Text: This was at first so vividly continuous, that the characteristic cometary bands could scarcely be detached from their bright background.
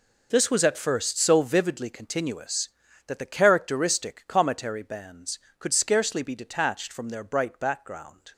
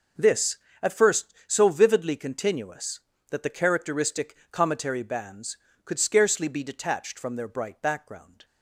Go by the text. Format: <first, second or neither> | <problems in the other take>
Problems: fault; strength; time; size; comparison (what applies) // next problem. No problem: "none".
first | skips "was"; at 0.6 s // pauses between "characteristic" and "cometary"; slight; at 4.3 s; 0.16 s long